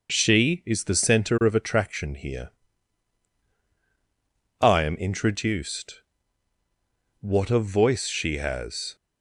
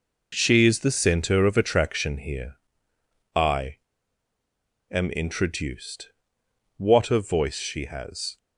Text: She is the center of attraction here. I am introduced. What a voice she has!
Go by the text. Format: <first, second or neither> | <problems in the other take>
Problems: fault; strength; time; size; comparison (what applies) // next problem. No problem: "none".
first | pauses between "I" and "am"; at 3.7 s; 1.1 s long